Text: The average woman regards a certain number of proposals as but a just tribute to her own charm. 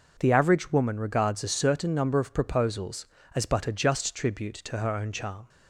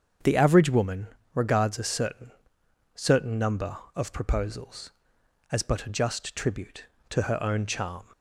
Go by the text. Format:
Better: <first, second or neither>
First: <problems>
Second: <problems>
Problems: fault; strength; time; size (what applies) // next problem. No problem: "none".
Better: first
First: none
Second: starts louder than the rest; until 1.5 s; 7 dB // pauses between "woman" and "regards"; slight; at 1.0 s; 0.26 s long // says "certain" twice; at 2.9 s